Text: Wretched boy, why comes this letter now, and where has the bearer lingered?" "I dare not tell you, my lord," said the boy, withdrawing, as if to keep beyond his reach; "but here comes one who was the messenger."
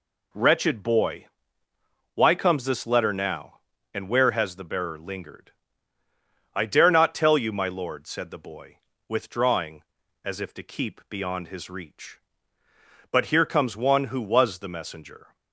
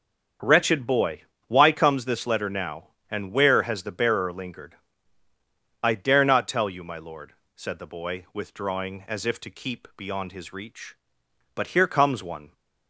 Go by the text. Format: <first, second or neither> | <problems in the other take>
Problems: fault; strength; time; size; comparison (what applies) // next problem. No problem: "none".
first | starts louder than the rest; strong; until 1.7 s; 7.5 dB // stops before "who was the messenger"; at 12.5 s